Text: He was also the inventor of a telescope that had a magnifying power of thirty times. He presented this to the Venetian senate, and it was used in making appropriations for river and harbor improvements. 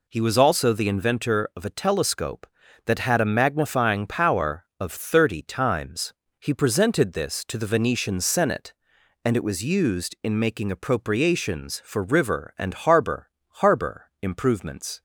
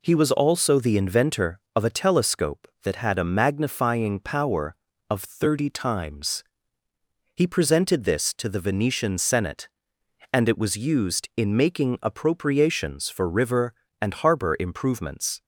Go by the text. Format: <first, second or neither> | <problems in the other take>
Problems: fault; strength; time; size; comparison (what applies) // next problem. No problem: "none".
second | says "harbor" twice; at 13.5 s